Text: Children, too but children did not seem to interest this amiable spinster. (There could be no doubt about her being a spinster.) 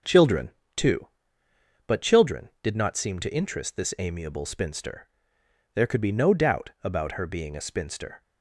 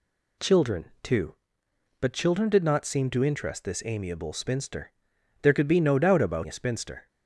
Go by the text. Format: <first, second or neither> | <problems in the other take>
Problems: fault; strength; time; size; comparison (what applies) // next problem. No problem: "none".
first | skips "her being"; at 6.4 s